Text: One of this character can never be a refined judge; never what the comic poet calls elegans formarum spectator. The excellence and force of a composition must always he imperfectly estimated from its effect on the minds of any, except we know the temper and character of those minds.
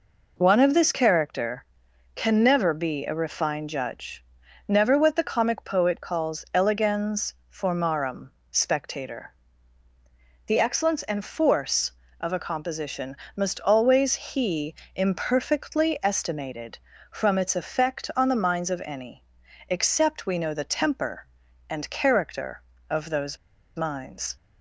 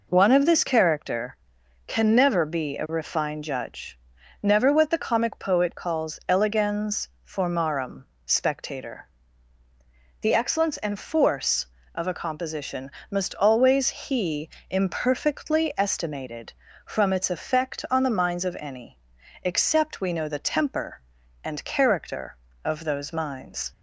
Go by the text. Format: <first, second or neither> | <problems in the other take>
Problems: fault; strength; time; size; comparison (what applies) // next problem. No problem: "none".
second | pauses between "elegans" and "formarum"; slight; at 7.3 s; 0.18 s long; slight in the second // pauses between "formarum" and "spectator"; slight; at 8.2 s; 0.22 s long; slight in the second // pauses between "composition" and "must"; slight; at 13.1 s; 0.20 s long; slight in the second // pauses between "he" and "imperfectly"; slight; at 14.7 s; 0.20 s long; slight in the second // pauses between "those" and "minds"; at 23.3 s; 0.40 s long